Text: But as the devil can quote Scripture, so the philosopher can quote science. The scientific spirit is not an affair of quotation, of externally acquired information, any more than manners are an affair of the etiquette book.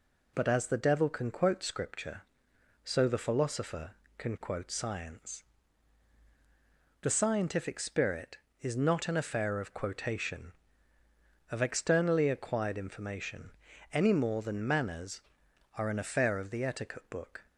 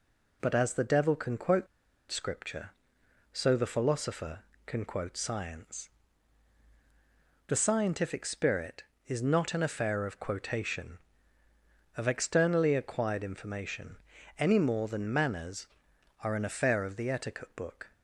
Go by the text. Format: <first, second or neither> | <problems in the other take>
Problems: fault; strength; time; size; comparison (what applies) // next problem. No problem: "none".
first | pauses between "quote" and "Scripture"; at 1.6 s; 0.44 s long